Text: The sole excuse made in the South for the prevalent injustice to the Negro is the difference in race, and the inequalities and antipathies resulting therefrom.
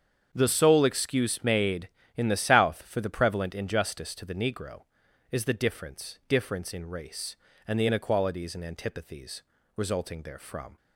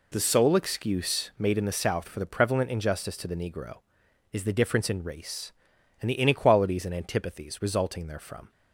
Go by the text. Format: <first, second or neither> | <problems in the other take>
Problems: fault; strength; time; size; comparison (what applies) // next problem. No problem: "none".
second | starts louder than the rest; strong; until 1.3 s; 7.5 dB // says "difference" twice; at 6.2 s // pauses between "antipathies" and "resulting"; slight; at 9.4 s; 0.34 s long